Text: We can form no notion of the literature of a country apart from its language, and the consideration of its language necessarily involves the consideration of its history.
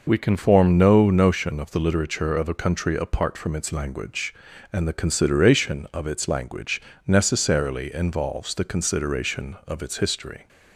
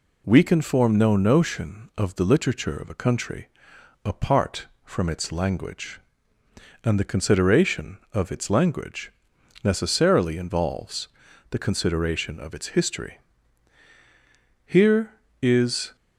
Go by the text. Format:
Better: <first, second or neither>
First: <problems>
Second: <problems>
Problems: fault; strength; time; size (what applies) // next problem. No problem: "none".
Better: first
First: pauses between "language" and "necessarily"; slight; at 6.8 s; 0.26 s long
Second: pauses between "country" and "apart"; noticeable; at 3.4 s; 0.56 s long // pauses between "language" and "necessarily"; noticeable; at 9.1 s; 0.52 s long // pauses between "involves" and "the"; at 11.0 s; 0.44 s long // goes on to say "Here is"; noticeable; from 14.6 s on; 1.3 s long